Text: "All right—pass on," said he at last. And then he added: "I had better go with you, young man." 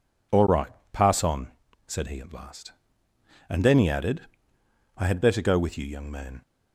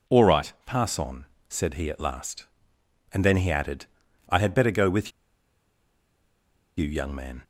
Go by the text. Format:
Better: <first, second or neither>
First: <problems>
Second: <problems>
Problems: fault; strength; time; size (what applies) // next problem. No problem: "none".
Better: first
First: none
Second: pauses between "with" and "you"; strong; at 5.1 s; 1.6 s long